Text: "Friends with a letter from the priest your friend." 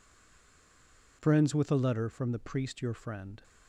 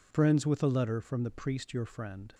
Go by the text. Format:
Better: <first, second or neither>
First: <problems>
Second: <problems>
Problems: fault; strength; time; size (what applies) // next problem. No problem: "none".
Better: second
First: stays silent before the first word; noticeable; until 1.2 s; 1.2 s long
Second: none